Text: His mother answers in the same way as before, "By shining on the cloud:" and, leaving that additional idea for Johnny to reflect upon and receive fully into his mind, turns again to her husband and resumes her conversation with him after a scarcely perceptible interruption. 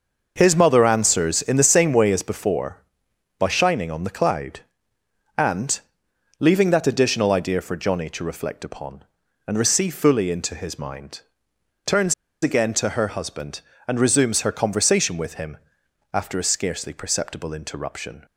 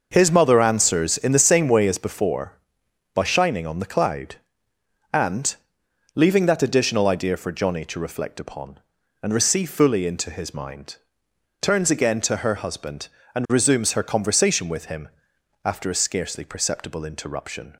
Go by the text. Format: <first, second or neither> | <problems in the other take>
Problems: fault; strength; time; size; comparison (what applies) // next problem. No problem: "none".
second | pauses between "turns" and "again"; slight; at 12.1 s; 0.29 s long // pauses between "him" and "after"; noticeable; at 15.5 s; 0.58 s long; noticeable in the second